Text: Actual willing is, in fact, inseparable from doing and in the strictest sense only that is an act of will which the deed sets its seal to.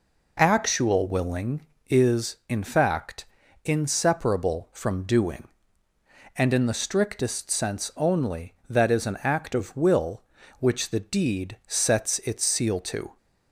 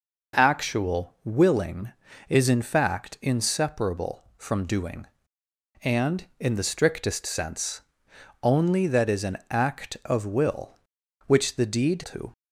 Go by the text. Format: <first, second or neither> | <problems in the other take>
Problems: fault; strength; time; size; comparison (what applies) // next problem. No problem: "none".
first | pauses between "sense" and "only"; noticeable; at 7.8 s; 0.60 s long // skips "sets its seal"; at 12.0 s